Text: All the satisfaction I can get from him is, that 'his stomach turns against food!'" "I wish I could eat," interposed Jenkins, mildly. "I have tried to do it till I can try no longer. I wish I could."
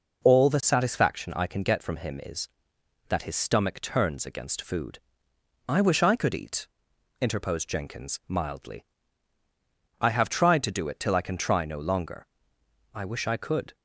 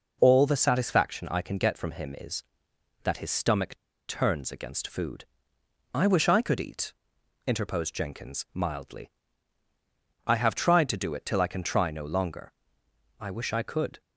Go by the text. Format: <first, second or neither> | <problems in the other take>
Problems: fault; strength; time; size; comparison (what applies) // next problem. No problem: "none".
first | pauses between "stomach" and "turns"; slight; at 3.7 s; 0.32 s long